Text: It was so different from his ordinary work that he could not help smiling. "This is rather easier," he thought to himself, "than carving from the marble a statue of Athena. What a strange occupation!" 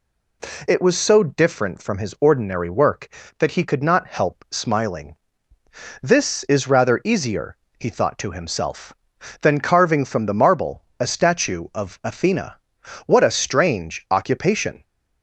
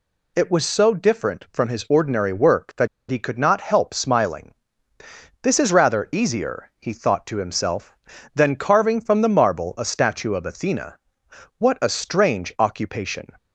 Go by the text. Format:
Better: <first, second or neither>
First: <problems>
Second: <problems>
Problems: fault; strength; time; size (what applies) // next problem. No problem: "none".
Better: first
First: none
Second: pauses between "that" and "he"; slight; at 2.8 s; 0.22 s long